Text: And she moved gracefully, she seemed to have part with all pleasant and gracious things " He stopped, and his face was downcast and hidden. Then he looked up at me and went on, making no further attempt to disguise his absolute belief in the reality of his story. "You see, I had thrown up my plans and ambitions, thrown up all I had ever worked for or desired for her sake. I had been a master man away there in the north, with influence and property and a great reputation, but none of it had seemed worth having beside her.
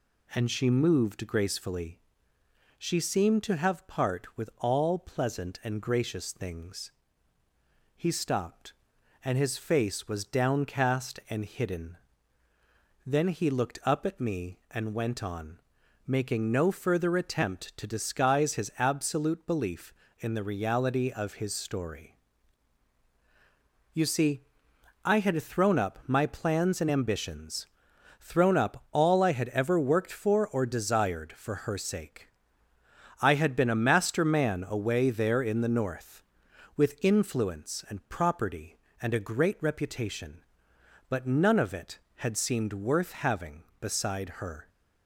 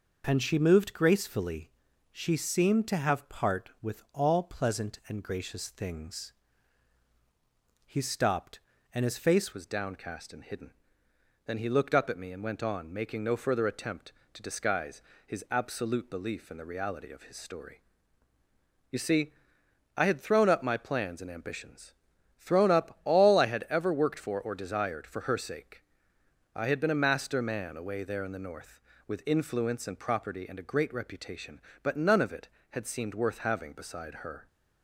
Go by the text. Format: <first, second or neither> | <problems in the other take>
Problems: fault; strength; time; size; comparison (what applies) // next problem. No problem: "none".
first | changes voice at "was"; from 9.5 s on; 24.9 s long // pauses between "disguise" and "his"; slight; at 15.0 s; 0.24 s long